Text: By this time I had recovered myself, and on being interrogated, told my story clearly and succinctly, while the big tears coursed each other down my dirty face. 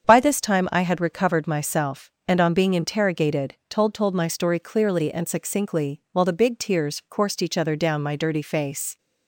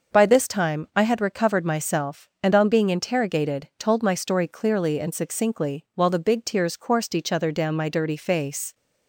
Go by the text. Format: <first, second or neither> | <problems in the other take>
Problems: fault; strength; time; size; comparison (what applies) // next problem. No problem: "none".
second | starts louder than the rest; strong; until 1.0 s; 7.5 dB; noticeable in the second // says "told" twice; at 3.9 s